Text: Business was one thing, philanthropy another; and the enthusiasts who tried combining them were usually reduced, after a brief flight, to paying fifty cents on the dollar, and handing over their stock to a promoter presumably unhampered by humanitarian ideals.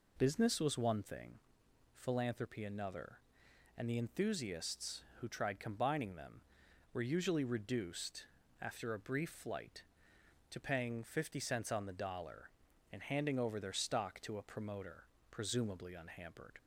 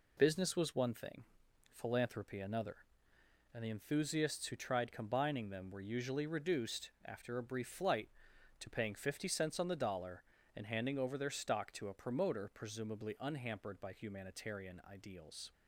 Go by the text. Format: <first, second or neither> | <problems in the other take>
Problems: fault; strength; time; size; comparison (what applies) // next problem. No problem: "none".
second | pauses between "promoter" and "presumably"; slight; at 15.0 s; 0.26 s long // stops before "by humanitarian ideals"; at 16.5 s